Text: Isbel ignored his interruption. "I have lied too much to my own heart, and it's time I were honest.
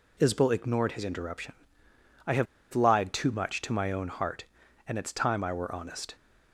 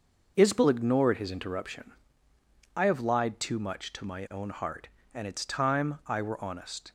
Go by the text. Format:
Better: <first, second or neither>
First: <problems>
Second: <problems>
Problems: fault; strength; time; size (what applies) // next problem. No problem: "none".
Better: second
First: pauses between "have" and "lied"; slight; at 2.4 s; 0.27 s long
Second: none